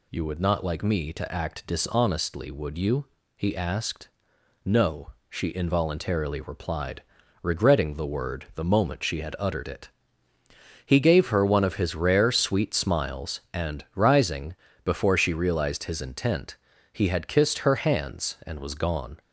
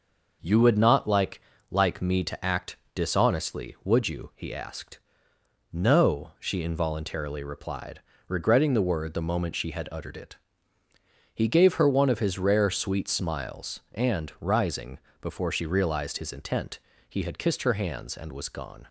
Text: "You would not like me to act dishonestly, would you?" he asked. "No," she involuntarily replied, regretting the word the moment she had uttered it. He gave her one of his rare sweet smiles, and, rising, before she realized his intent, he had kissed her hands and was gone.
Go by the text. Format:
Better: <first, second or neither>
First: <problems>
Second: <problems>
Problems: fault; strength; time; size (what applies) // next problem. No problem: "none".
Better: first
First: none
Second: says "like" twice; at 1.6 s // pauses between "act" and "dishonestly"; slight; at 2.7 s; 0.16 s long